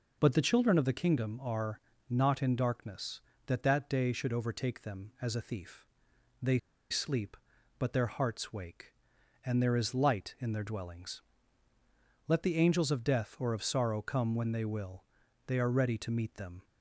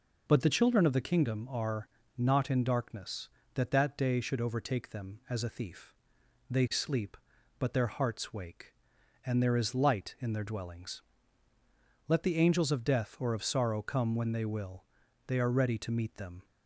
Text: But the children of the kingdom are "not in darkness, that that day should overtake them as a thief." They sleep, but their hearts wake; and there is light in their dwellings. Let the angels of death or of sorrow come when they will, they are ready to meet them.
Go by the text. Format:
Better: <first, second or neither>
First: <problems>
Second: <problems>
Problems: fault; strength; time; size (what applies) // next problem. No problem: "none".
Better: second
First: pauses between "are" and "not"; slight; at 1.7 s; 0.30 s long // pauses between "They" and "sleep"; slight; at 6.5 s; 0.31 s long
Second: pauses between "are" and "not"; slight; at 1.8 s; 0.30 s long